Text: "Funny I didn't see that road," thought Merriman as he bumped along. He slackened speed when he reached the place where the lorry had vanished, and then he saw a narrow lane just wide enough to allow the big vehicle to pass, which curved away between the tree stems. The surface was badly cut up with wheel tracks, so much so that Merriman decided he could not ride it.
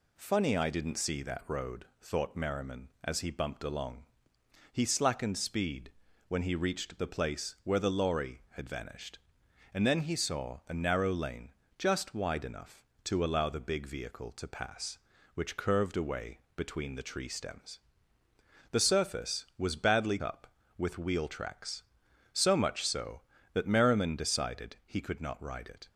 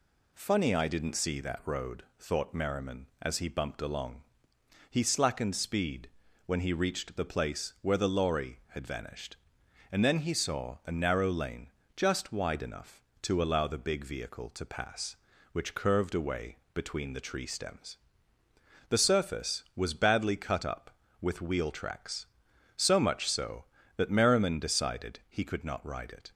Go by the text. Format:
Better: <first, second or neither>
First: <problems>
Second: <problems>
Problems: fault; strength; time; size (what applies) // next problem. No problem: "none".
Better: second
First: pauses between "speed" and "when"; slight; at 5.9 s; 0.36 s long // pauses between "lane" and "just"; slight; at 11.5 s; 0.24 s long // pauses between "away" and "between"; slight; at 16.3 s; 0.18 s long // skips "cut"; at 20.2 s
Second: pauses between "speed" and "when"; slight; at 6.0 s; 0.36 s long // pauses between "lane" and "just"; slight; at 11.7 s; 0.24 s long // pauses between "away" and "between"; slight; at 16.5 s; 0.18 s long